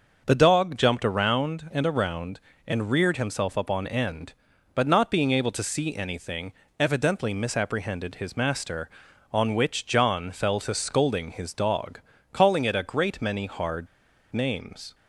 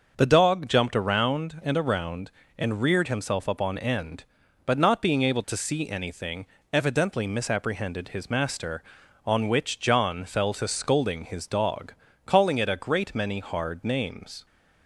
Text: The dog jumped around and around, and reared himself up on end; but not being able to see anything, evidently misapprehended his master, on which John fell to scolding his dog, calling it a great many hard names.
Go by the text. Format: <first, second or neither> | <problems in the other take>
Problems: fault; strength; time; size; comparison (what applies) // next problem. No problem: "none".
second | starts louder than the rest; noticeable; until 1.2 s; 6 dB; noticeable in the second // pauses between "hard" and "names"; at 13.8 s; 0.45 s long